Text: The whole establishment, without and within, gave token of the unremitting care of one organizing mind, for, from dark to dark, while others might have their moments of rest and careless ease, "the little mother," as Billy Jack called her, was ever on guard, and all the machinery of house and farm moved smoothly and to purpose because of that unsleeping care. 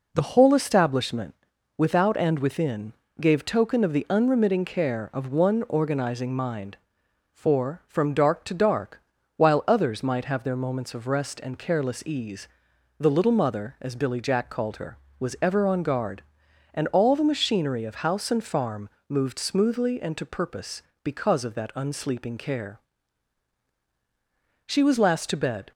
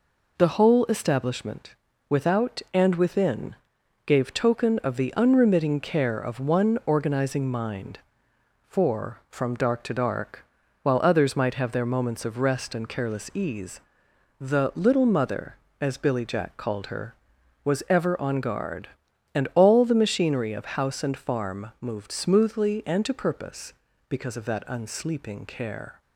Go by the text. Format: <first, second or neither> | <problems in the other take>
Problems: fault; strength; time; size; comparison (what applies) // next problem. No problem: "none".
second | pauses between "farm" and "moved"; slight; at 18.8 s; 0.18 s long // goes on to say "She was last to bed"; noticeable; from 24.6 s on; 1.0 s long